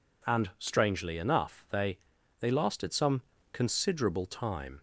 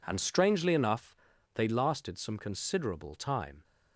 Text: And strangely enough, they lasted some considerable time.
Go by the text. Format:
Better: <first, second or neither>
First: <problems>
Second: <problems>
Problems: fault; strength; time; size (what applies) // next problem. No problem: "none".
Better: second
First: says "they" twice; at 2.3 s // pauses between "some" and "considerable"; slight; at 3.2 s; 0.28 s long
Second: none